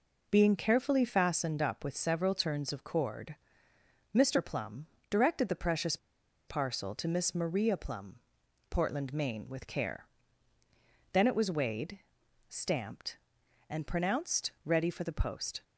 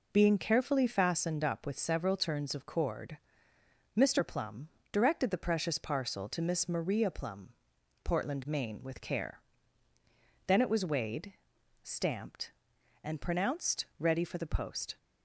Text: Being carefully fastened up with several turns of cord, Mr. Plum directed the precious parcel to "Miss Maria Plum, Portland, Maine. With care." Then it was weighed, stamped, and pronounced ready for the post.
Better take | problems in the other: second | pauses between "Plum" and "directed"; slight; at 4.8 s; 0.24 s long; slight in the second // pauses between "precious" and "parcel"; noticeable; at 5.9 s; 0.51 s long

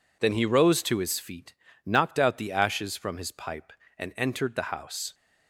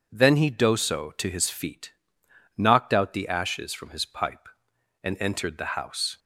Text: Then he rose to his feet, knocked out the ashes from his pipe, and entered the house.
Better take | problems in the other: first | says "doso" for "rose"; at 0.5 s

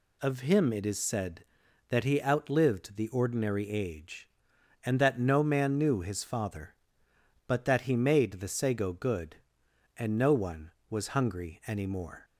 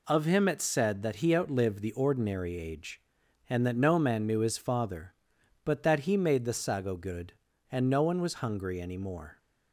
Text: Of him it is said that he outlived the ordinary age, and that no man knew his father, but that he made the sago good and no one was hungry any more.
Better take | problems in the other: first | skips "is"; at 0.6 s

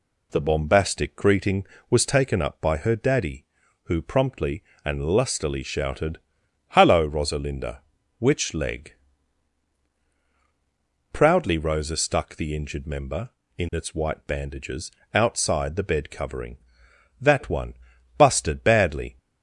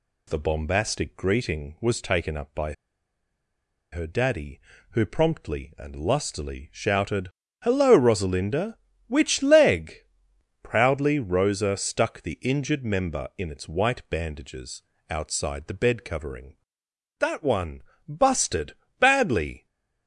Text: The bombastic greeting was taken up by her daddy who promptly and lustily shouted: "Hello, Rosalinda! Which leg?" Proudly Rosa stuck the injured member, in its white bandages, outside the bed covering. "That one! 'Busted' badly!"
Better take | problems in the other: first | pauses between "by" and "her"; at 2.7 s; 1.1 s long // pauses between "Busted" and "badly"; slight; at 18.7 s; 0.24 s long

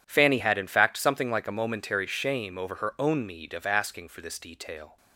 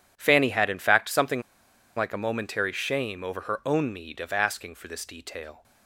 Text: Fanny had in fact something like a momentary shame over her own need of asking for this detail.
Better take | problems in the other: first | pauses between "something" and "like"; noticeable; at 1.4 s; 0.55 s long

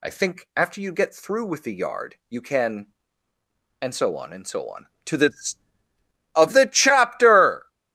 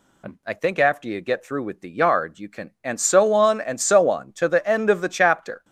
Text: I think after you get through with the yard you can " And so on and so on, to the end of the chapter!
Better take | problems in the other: second | skips "end"; at 5.8 s

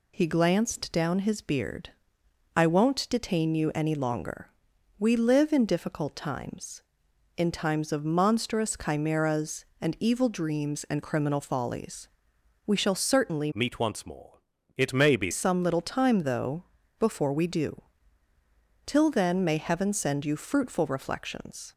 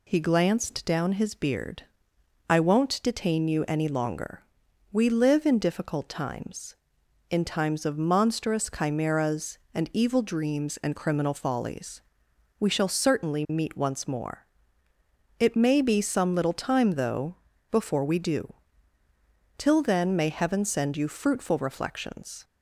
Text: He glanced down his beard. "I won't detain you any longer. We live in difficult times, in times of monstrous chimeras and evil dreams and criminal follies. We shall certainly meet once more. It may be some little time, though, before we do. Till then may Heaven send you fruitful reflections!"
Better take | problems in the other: second | changes voice from "meet" to "be"; from 13.5 to 15.3 s; 1.8 s long

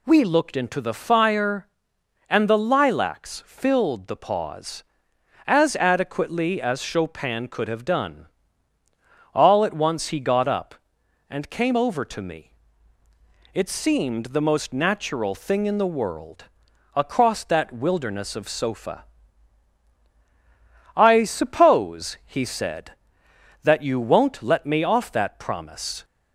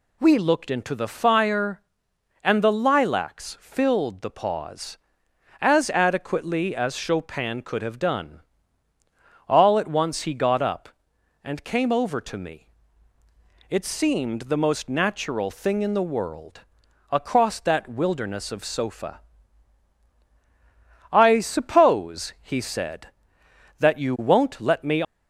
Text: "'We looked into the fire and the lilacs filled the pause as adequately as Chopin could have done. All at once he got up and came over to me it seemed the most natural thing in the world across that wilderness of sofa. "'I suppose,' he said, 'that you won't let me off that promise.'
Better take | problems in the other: first | pauses between "me" and "it"; at 12.6 s; 1.0 s long; also in the first // pauses between "world" and "across"; noticeable; at 16.6 s; 0.50 s long; noticeable in the first // stops before "off that promise"; at 25.0 s

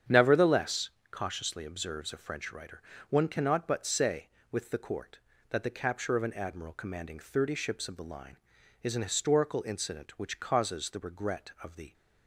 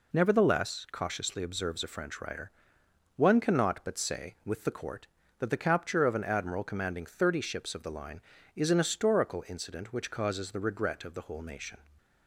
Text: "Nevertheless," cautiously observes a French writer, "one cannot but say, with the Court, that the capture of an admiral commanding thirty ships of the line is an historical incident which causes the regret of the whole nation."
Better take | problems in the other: second | starts louder than the rest; strong; until 1.3 s; 8.5 dB // stops before "whole nation"; at 11.9 s

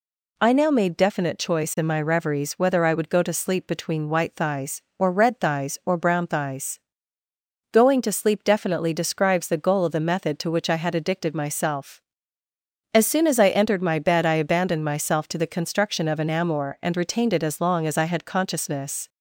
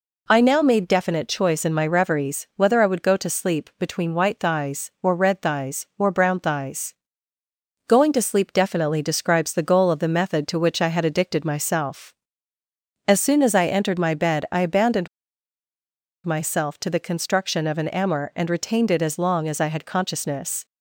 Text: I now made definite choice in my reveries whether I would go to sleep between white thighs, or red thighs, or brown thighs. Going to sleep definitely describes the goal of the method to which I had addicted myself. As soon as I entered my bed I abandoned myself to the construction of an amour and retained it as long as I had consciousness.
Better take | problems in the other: first | pauses between "abandoned" and "myself"; at 15.0 s; 1.1 s long

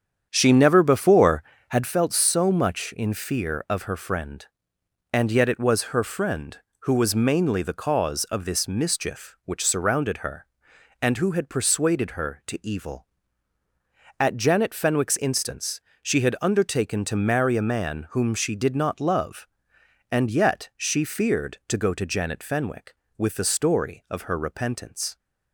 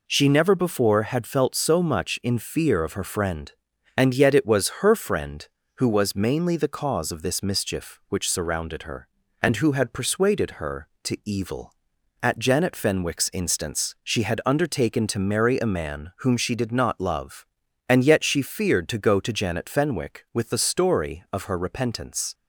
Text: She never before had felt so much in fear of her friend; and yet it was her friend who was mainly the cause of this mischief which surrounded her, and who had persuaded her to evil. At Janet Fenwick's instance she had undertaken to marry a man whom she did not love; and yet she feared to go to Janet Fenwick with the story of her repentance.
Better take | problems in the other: second | starts louder than the rest; strong; until 1.9 s; 8.5 dB // pauses between "instance" and "she"; slight; at 15.7 s; 0.22 s long

